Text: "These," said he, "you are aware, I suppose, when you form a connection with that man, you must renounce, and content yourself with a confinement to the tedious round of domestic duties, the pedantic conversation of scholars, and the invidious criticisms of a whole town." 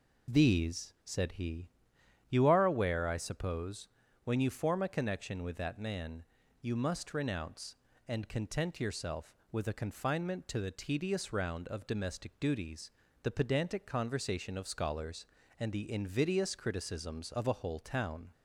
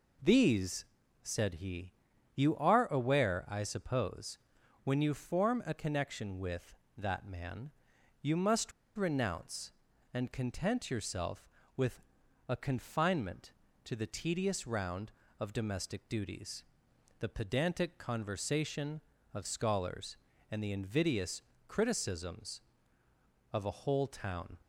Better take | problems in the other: first | pauses between "must" and "renounce"; slight; at 8.7 s; 0.26 s long // pauses between "with" and "a"; at 12.0 s; 0.44 s long // pauses between "invidious" and "criticisms"; slight; at 21.4 s; 0.26 s long

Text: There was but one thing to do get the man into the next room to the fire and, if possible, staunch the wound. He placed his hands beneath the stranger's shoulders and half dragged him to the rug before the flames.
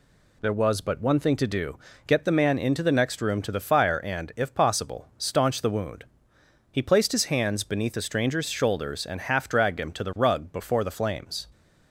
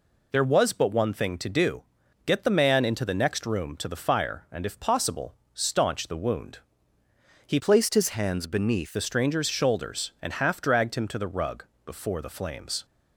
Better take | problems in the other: first | pauses between "do" and "get"; at 1.8 s; 0.44 s long; slight in the first // changes voice from "placed" to "beneath"; from 7.5 to 8.9 s; 1.4 s long // pauses between "rug" and "before"; slight; at 11.6 s; 0.22 s long

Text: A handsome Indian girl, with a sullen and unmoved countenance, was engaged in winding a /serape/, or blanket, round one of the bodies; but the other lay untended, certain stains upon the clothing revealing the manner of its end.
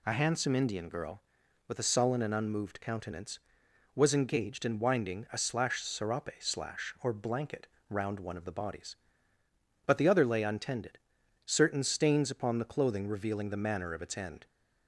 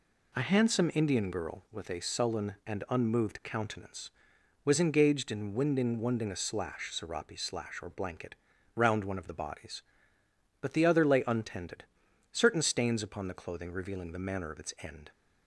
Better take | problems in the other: first | says "winding" twice; at 5.9 s

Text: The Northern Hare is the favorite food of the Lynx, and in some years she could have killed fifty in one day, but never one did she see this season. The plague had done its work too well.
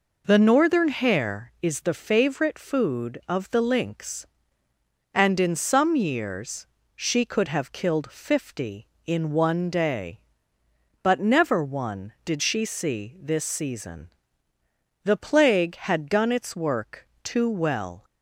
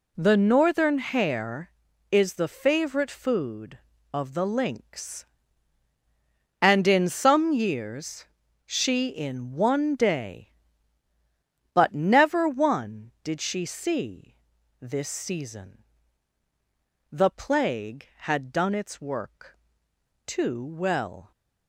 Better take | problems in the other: first | pauses between "years" and "she"; at 8.2 s; 0.42 s long; slight in the first // skips "could have killed fifty"; at 9.0 s // pauses between "see" and "this"; at 14.3 s; 0.44 s long // pauses between "work" and "too"; noticeable; at 19.5 s; 0.68 s long; slight in the first

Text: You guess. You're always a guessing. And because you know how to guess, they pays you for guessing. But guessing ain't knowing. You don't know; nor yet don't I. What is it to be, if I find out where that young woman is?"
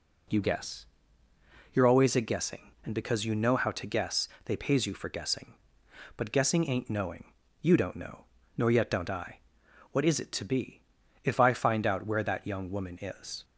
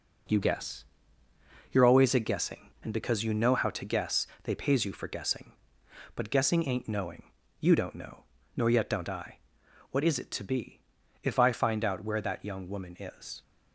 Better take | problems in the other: first | gets quieter; throughout; 7 dB

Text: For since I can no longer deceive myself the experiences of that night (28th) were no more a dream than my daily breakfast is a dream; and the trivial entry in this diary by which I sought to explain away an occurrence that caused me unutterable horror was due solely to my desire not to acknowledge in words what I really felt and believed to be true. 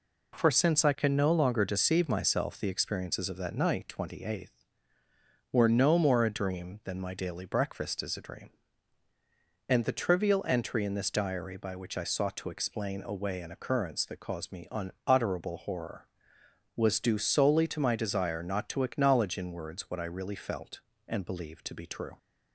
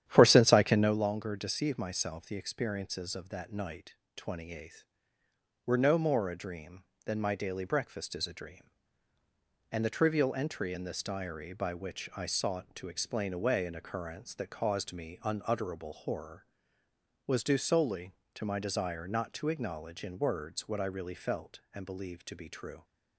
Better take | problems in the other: first | starts louder than the rest; strong; until 1.0 s; 10.5 dB

